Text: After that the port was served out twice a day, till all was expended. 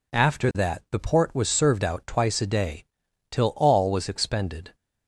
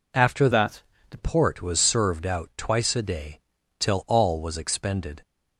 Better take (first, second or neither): first